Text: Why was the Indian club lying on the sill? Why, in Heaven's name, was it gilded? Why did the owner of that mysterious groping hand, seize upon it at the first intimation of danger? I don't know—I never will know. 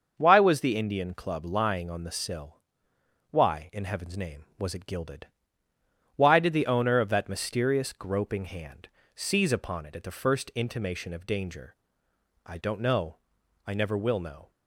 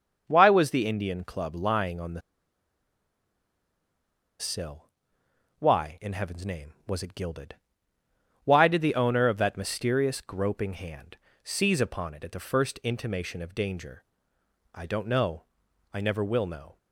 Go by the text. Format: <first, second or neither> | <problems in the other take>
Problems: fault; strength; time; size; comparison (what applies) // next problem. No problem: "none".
first | starts louder than the rest; until 1.2 s; 6.5 dB; also in the first // pauses between "the" and "sill"; strong; at 2.2 s; 2.1 s long